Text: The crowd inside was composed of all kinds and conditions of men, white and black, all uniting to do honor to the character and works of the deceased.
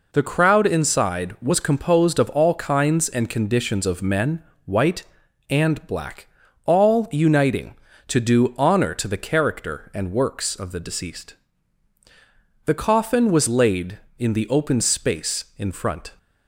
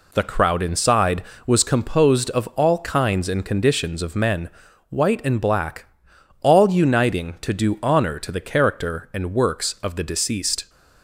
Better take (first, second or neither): second